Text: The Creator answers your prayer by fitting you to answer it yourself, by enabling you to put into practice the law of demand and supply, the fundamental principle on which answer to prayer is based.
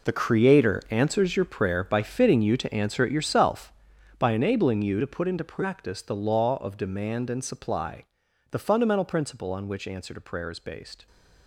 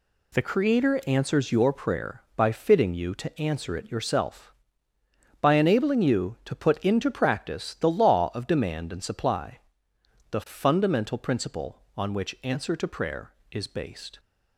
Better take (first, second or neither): second